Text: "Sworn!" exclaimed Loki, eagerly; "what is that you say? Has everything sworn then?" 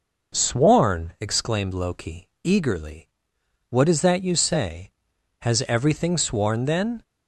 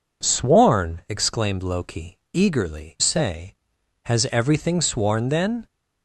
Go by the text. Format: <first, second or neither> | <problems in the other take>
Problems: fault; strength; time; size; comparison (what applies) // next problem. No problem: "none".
first | skips "what is that you"; at 2.9 s